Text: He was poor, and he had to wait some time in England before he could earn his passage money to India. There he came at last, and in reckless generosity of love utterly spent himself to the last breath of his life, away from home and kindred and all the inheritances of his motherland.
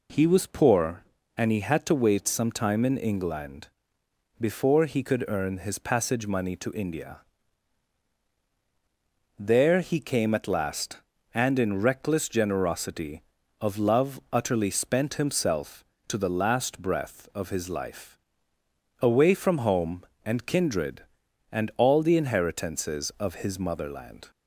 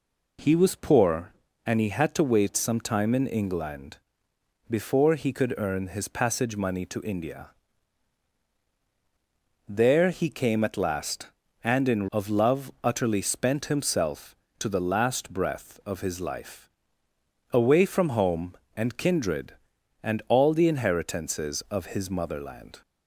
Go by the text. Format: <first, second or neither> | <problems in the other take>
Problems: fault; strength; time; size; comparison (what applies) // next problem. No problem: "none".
first | pauses between "England" and "before"; noticeable; at 3.9 s; 0.72 s long; noticeable in the first // skips "reckless generosity"; at 12.0 s